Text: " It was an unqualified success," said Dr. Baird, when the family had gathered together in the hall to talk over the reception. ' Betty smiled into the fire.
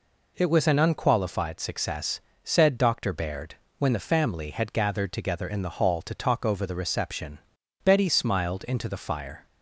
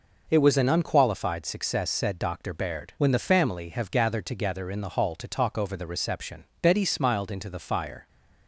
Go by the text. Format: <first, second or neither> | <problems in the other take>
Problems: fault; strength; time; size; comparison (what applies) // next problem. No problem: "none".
first | says "have" for "had"; at 3.6 s